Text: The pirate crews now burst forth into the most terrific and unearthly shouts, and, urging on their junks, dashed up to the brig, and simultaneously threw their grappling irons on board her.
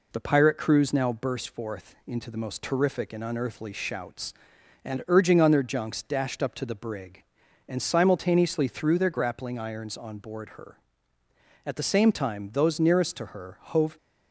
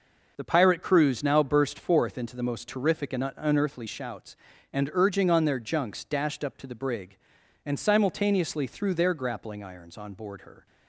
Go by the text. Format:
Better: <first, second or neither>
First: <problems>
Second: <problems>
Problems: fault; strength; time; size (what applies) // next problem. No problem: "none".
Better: second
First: goes on to say "At the same time those nearest to her hove"; strong; from 11.6 s on; 2.3 s long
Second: none